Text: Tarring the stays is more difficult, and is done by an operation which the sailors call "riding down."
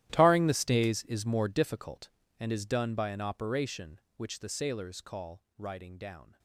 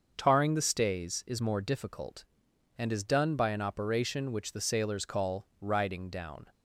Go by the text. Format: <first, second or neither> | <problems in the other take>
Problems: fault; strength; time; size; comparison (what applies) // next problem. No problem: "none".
second | gets quieter; strong; throughout; 19 dB // starts louder than the rest; strong; until 1.1 s; 13.5 dB; also in the second